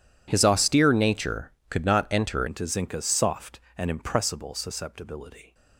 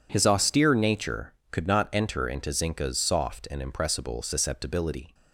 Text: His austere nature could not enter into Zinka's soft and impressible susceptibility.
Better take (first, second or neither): second